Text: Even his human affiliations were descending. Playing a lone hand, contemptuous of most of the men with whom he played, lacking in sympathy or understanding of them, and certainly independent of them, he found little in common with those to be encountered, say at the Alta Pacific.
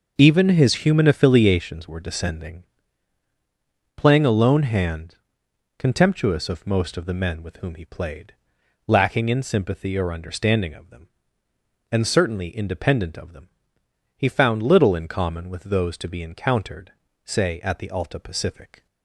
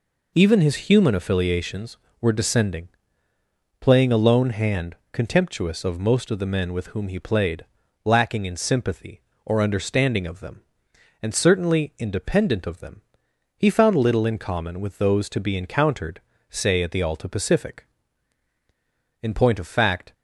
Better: first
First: none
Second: goes on to say "In point of fact"; noticeable; from 19.2 s on; 0.92 s long

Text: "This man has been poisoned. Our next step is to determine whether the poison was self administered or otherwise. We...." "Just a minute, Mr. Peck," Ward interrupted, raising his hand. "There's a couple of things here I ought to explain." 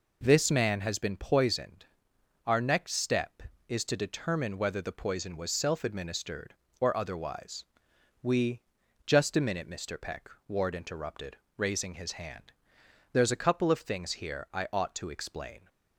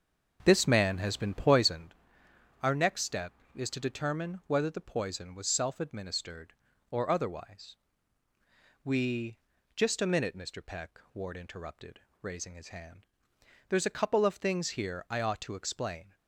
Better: first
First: none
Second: starts louder than the rest; until 1.9 s; 6.5 dB

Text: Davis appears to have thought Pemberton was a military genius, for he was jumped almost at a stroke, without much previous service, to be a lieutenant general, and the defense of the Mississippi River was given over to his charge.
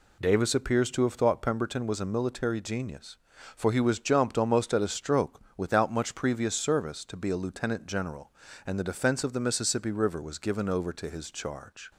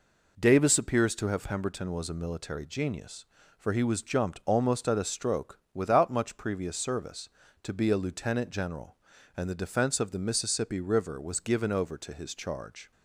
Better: first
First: none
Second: skips "thought"; at 1.4 s

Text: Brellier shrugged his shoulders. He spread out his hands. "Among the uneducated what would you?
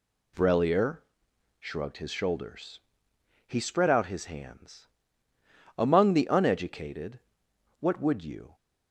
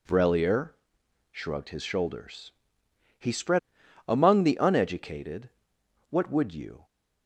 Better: first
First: pauses between "Brellier" and "shrugged"; noticeable; at 1.0 s; 0.58 s long // pauses between "uneducated" and "what"; noticeable; at 7.1 s; 0.62 s long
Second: pauses between "Brellier" and "shrugged"; noticeable; at 0.7 s; 0.58 s long // skips "out his hands"; at 3.8 s // pauses between "uneducated" and "what"; noticeable; at 5.4 s; 0.62 s long

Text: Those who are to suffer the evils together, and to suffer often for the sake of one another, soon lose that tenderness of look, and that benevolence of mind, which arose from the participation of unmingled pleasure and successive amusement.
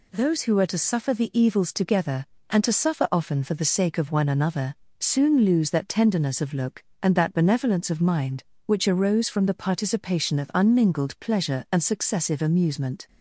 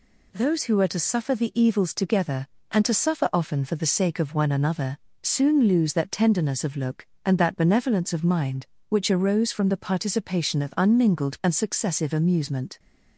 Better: first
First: none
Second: skips "pleasure"; at 11.4 s

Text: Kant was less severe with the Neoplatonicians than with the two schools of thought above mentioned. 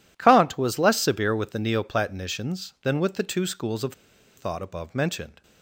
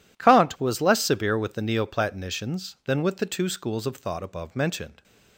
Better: second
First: pauses between "of" and "thought"; at 3.9 s; 0.44 s long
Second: none

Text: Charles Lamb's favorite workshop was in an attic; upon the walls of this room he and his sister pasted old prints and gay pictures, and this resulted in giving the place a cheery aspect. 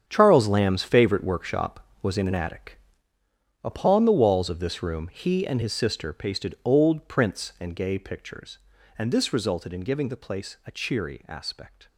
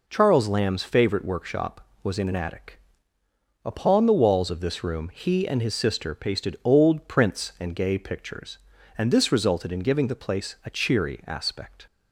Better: second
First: gets quieter; strong; throughout; 13 dB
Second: none

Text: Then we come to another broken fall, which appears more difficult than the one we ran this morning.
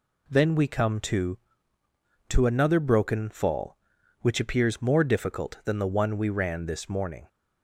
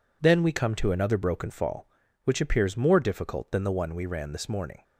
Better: second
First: says "to" twice; at 2.2 s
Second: none

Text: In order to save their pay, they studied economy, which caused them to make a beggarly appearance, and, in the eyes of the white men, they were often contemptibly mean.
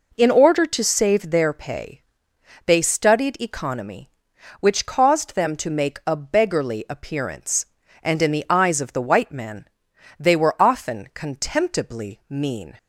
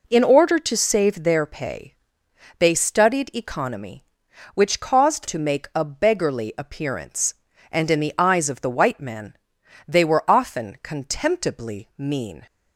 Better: first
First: none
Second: skips "them"; at 5.2 s

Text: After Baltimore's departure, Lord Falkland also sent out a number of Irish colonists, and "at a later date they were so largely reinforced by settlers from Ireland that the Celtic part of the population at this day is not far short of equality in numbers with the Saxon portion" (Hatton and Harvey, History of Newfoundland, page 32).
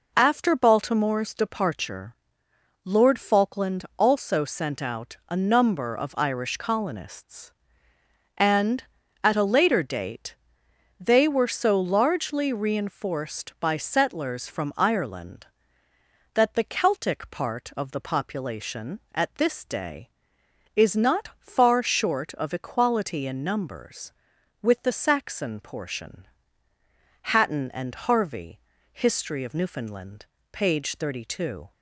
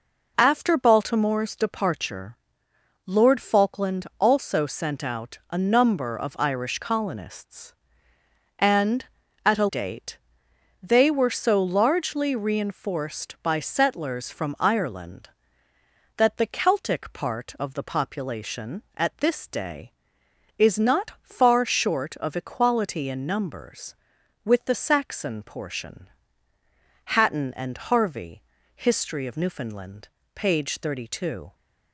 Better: first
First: pauses between "date" and "they"; noticeable; at 10.3 s; 0.64 s long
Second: skips "later"; at 9.6 s // pauses between "date" and "they"; noticeable; at 10.1 s; 0.64 s long

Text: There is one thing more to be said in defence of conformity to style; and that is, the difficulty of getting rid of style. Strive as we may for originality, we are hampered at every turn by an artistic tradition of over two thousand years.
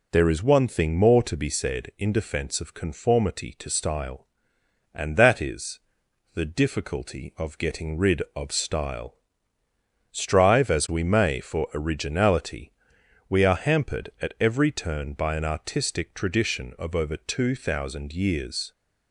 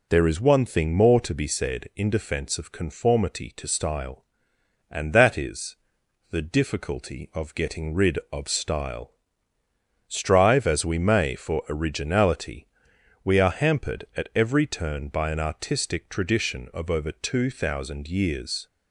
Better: neither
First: none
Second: none

